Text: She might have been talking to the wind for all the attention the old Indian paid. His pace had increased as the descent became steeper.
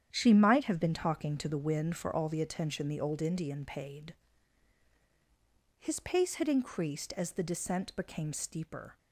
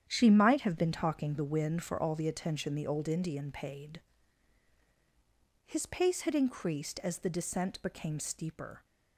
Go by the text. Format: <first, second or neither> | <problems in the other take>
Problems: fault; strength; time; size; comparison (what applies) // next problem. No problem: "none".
first | starts louder than the rest; strong; until 1.0 s; 9 dB; strong in the first // skips "to"; at 1.3 s